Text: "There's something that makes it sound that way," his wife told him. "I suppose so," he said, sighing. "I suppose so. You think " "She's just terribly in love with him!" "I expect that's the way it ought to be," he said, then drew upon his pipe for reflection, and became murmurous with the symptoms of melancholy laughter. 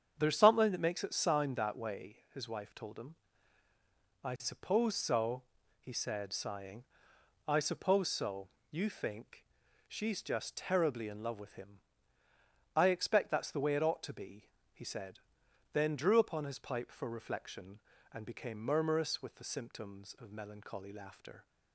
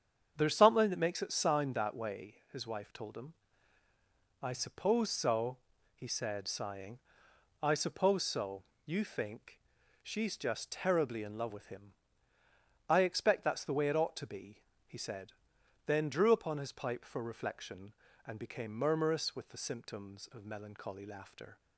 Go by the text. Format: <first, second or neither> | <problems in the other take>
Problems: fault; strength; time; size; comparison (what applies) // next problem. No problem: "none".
neither | starts louder than the rest; strong; the same in both